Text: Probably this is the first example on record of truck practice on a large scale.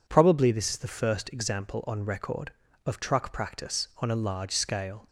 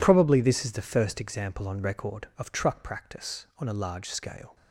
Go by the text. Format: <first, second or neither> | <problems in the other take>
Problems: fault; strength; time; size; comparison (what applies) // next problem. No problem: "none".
neither | none